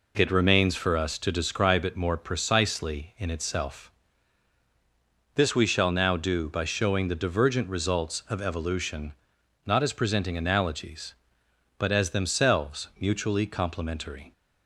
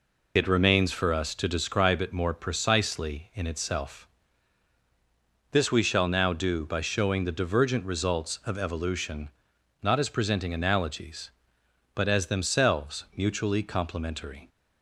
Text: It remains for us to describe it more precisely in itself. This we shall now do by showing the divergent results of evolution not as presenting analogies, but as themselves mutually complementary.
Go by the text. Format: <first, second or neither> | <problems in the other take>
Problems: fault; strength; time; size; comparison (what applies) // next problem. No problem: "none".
first | loses the start of "It"; at 0.3 s; 40 ms // pauses between "evolution" and "not"; noticeable; at 9.2 s; 0.54 s long; noticeable in the first